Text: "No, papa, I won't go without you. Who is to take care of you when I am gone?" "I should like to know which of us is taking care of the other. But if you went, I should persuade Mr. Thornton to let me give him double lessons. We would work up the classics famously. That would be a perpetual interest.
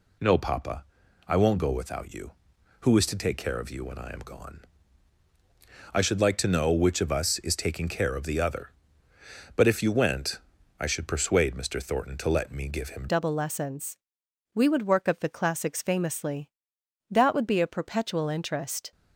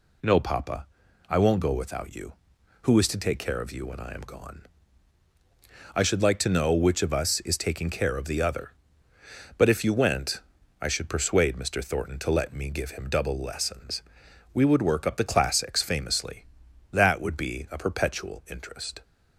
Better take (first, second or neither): second